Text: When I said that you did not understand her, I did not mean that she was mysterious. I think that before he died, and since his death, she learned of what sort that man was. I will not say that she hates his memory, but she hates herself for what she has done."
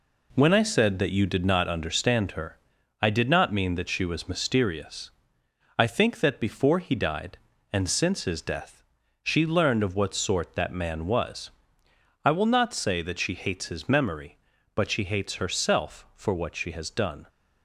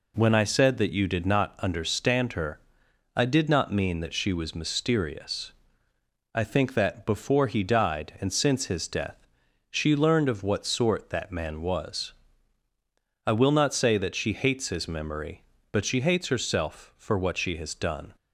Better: second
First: gets quieter; throughout; 6 dB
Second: none

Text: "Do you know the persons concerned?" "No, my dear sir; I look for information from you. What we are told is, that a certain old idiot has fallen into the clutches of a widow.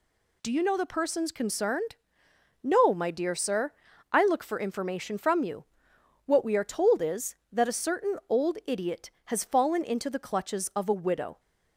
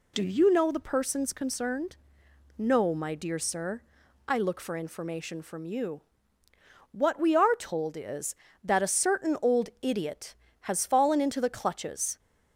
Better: first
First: none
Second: stops before "of a widow"; at 12.1 s

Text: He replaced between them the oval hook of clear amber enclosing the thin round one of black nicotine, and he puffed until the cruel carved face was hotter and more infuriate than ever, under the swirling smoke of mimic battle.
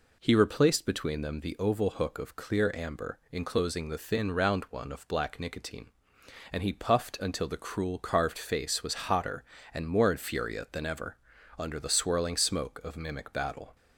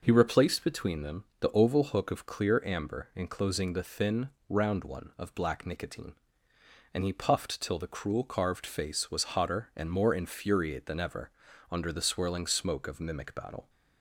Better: first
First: none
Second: pauses between "them" and "the"; slight; at 1.2 s; 0.16 s long // pauses between "thin" and "round"; slight; at 4.2 s; 0.22 s long // says "till" for "until"; at 7.6 s

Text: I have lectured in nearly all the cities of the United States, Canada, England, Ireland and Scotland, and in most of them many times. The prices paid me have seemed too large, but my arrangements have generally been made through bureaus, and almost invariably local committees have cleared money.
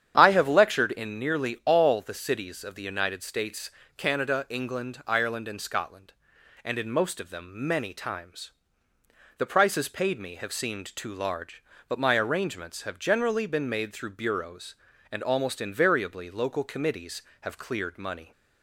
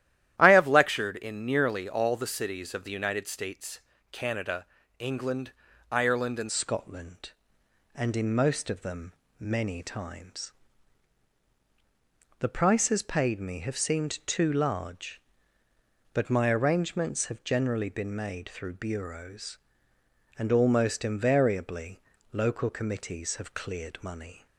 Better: first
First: starts louder than the rest; strong; until 1.1 s; 9 dB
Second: starts louder than the rest; strong; until 1.3 s; 12.5 dB // changes voice at "Scotland"; from 6.4 s on; 18.0 s long // pauses between "them" and "many"; slight; at 9.1 s; 0.26 s long // pauses between "invariably" and "local"; slight; at 21.9 s; 0.32 s long

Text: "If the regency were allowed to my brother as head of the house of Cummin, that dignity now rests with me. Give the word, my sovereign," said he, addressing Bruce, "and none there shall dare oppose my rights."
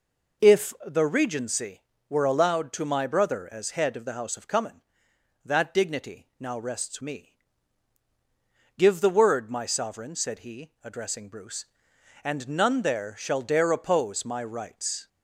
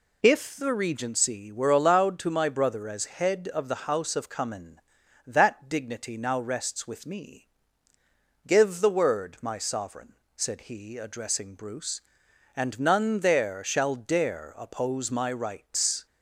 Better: second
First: skips "with"; at 7.0 s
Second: none

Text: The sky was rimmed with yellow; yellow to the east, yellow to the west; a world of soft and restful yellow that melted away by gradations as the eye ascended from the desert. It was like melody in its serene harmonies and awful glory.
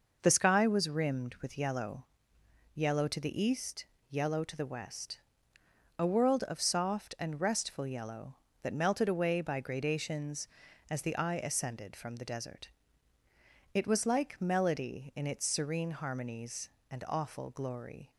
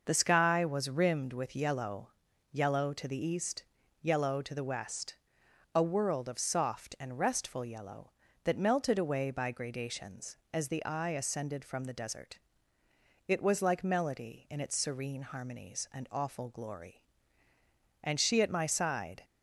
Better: first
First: none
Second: goes on to say "And she at my side"; noticeable; from 18.0 s on; 1.2 s long

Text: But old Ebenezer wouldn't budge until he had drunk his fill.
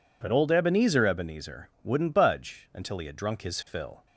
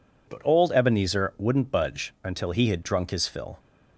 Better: second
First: says "Ebenezer" twice; at 1.0 s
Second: none

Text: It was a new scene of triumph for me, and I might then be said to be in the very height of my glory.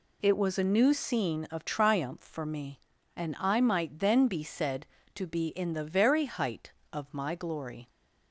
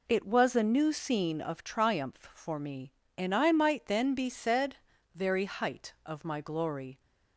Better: first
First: none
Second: skips "to be in the"; at 4.9 s

